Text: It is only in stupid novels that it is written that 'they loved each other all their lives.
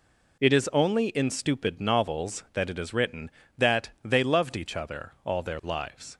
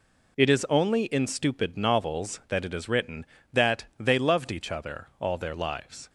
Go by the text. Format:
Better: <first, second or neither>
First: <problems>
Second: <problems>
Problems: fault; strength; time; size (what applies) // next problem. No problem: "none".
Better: neither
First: none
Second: none